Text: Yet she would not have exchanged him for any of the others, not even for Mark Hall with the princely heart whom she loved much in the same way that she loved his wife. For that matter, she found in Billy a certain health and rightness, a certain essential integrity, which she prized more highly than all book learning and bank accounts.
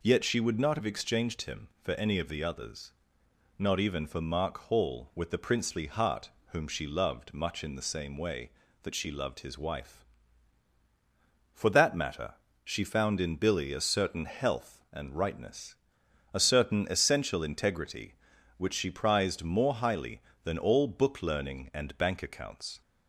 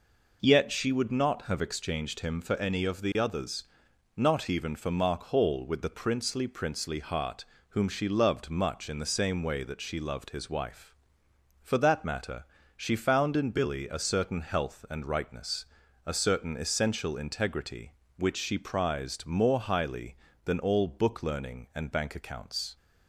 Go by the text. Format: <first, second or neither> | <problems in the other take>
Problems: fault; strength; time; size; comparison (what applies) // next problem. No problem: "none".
first | says "princely" twice; at 6.4 s // pauses between "heart" and "whom"; slight; at 7.4 s; 0.24 s long; slight in the first